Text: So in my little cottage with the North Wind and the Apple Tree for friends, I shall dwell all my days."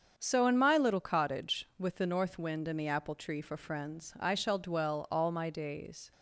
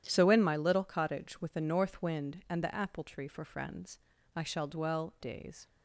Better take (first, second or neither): first